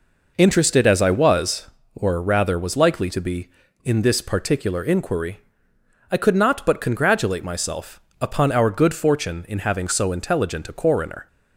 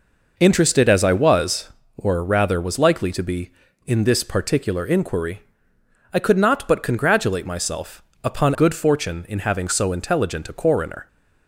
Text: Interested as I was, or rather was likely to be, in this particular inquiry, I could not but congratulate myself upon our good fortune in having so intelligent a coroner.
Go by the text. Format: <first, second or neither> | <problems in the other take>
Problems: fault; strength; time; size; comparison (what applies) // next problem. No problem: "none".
first | pauses between "myself" and "upon"; slight; at 8.0 s; 0.20 s long; slight in the first // skips "our"; at 8.5 s